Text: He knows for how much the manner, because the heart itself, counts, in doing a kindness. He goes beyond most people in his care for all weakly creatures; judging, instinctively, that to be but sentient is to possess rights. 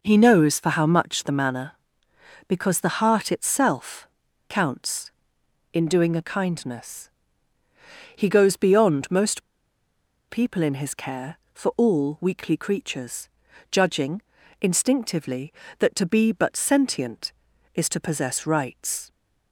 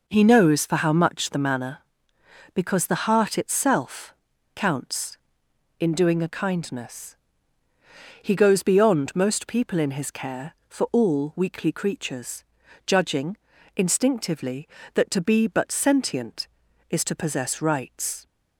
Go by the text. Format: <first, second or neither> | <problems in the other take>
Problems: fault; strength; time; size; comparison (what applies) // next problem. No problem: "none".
second | pauses between "most" and "people"; noticeable; at 9.4 s; 0.89 s long